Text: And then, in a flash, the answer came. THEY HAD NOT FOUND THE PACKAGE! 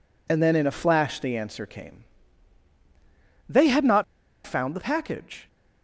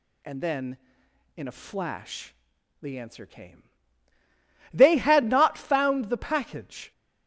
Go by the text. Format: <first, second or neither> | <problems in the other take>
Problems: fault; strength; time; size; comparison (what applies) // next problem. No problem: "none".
second | pauses between "NOT" and "FOUND"; at 4.0 s; 0.43 s long